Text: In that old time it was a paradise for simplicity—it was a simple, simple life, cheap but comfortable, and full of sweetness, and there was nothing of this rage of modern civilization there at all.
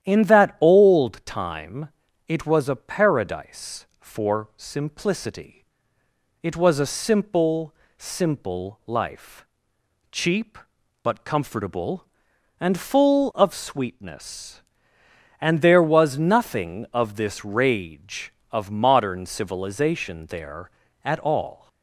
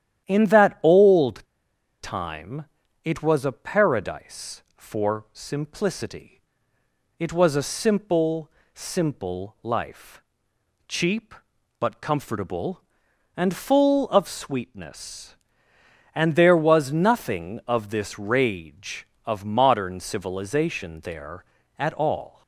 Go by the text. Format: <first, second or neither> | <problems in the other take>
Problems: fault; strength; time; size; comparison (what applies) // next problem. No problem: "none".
first | starts louder than the rest; strong; until 1.3 s; 10.5 dB; strong in the first // pauses between "old" and "time"; noticeable; at 1.4 s; 0.58 s long // pauses between "time" and "it"; at 2.6 s; 0.38 s long; also in the first